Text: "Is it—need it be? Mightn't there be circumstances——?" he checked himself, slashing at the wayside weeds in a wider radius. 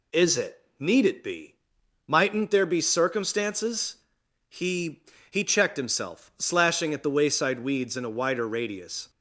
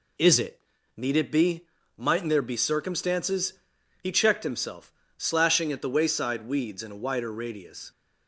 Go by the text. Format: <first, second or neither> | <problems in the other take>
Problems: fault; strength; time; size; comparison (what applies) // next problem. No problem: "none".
second | says "he" twice; at 5.2 s